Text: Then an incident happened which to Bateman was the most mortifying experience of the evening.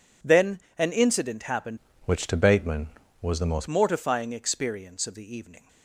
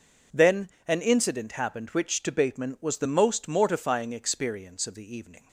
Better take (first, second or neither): second